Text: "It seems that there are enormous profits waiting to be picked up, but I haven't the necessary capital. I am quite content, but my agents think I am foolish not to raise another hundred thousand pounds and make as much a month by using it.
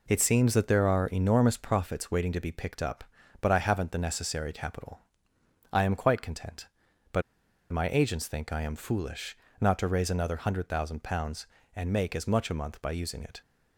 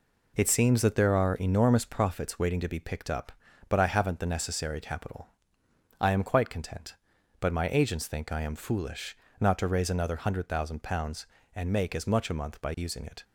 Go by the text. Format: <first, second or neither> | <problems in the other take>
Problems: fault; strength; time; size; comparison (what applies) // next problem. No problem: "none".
second | pauses between "but" and "my"; noticeable; at 7.2 s; 0.50 s long // pauses between "foolish" and "not"; slight; at 9.3 s; 0.22 s long; slight in the second